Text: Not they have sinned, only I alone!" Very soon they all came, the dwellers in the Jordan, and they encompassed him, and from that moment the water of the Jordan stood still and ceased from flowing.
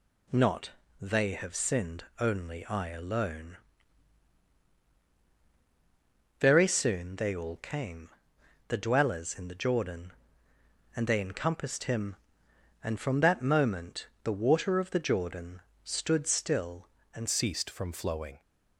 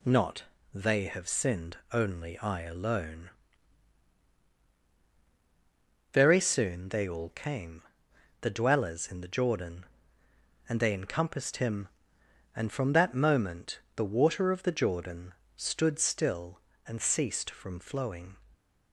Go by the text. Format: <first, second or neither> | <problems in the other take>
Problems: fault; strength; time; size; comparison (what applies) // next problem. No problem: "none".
second | pauses between "Not" and "they"; slight; at 0.7 s; 0.30 s long; slight in the second // pauses between "moment" and "the"; slight; at 14.0 s; 0.16 s long; slight in the second // pauses between "Jordan" and "stood"; slight; at 15.6 s; 0.20 s long; slight in the second // changes voice at "ceased"; from 17.2 s on; 1.2 s long